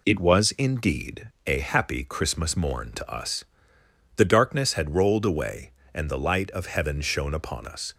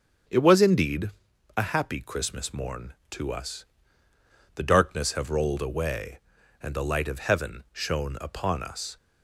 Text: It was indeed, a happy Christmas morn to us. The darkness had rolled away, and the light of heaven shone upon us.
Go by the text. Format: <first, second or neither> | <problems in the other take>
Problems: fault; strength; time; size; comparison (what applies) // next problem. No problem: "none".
first | starts louder than the rest; strong; until 1.7 s; 7.5 dB // says "have" for "had"; at 5.1 s